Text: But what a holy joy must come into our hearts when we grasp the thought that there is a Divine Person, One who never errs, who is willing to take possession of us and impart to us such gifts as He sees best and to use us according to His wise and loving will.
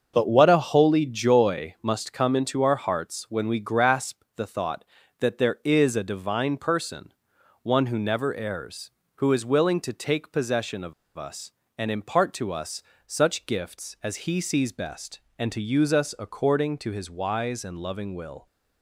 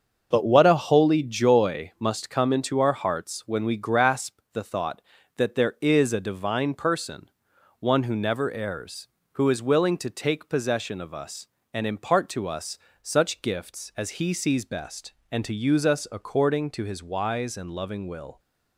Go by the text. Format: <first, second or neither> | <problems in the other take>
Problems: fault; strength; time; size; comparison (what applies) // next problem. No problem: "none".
second | starts louder than the rest; until 1.1 s; 6.5 dB; also in the second // pauses between "of" and "us"; slight; at 10.9 s; 0.24 s long // pauses between "us" and "such"; slight; at 12.8 s; 0.24 s long; slight in the second